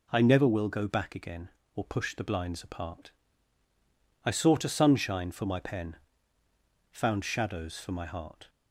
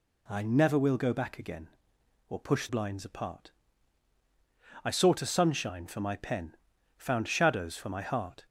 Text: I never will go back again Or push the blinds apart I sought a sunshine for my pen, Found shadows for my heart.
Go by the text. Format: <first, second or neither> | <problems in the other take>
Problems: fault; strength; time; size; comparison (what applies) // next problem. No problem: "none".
first | skips "the"; at 2.6 s // pauses between "apart" and "I"; strong; at 3.5 s; 1.3 s long; also in the first